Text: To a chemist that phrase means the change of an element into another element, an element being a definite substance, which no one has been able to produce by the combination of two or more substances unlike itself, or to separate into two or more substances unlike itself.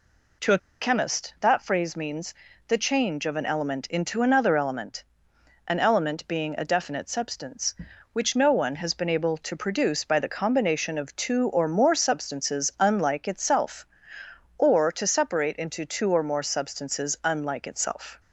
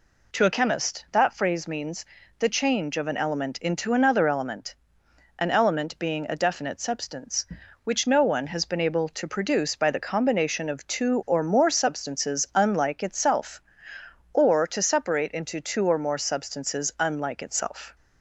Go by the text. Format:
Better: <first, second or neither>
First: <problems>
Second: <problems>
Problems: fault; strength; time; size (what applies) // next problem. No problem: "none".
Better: second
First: pauses between "a" and "chemist"; slight; at 0.5 s; 0.22 s long // pauses between "means" and "the"; slight; at 2.3 s; 0.32 s long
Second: pauses between "means" and "the"; slight; at 2.0 s; 0.32 s long